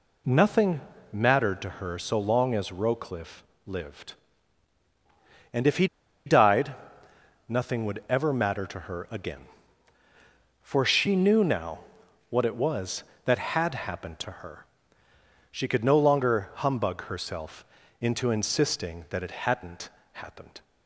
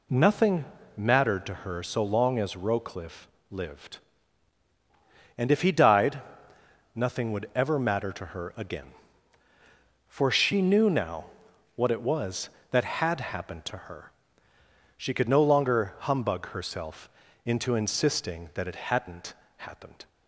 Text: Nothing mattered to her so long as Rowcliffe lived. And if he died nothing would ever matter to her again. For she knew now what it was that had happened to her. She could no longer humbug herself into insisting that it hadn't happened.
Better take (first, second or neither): second